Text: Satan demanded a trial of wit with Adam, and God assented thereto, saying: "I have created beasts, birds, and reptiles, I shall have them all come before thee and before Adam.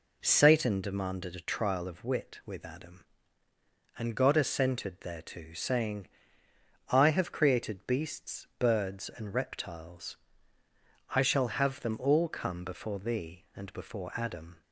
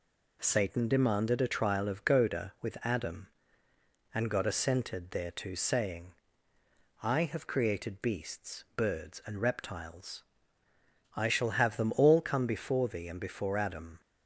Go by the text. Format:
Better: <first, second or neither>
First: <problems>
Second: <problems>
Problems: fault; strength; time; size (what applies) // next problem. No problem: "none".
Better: first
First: none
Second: says "goda" for "wit"; at 2.0 s